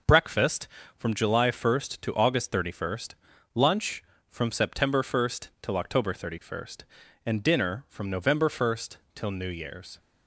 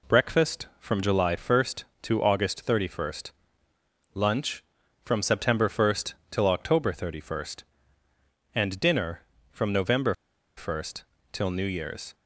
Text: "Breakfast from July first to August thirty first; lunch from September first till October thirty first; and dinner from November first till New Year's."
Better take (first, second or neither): first